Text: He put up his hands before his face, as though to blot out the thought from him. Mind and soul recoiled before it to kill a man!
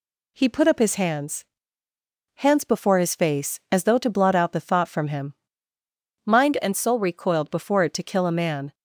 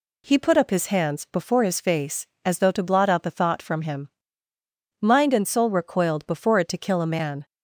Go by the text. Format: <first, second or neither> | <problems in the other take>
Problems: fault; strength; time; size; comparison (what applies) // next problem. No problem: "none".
second | says "hands" twice; at 2.3 s